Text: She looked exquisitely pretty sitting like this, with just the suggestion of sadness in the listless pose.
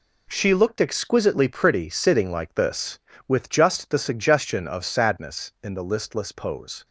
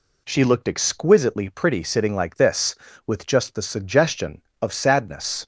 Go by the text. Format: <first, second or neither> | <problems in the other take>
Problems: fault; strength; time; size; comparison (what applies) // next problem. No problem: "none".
first | stops before "in the listless pose"; at 5.4 s